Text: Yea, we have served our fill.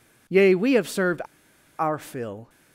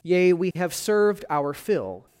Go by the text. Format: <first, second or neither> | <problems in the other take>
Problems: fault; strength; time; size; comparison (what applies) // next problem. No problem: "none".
second | pauses between "served" and "our"; noticeable; at 1.2 s; 0.57 s long